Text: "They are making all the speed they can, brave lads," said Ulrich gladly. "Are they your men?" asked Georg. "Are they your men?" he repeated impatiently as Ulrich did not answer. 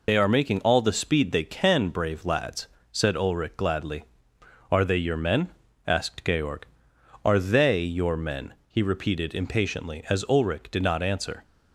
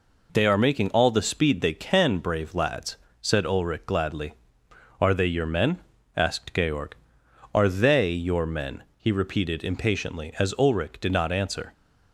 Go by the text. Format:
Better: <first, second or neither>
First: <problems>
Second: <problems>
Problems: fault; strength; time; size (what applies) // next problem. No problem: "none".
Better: second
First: loses the start of "They"; at 0.0 s; 80 ms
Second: none